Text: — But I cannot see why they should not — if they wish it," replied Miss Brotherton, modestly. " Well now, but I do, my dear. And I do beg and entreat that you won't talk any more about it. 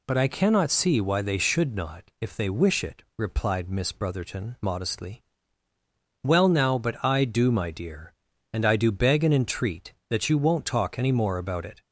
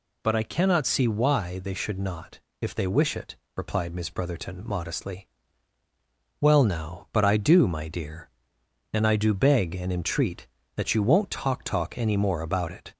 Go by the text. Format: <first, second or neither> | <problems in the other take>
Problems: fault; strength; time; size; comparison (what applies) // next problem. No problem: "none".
first | says "talk" twice; at 11.6 s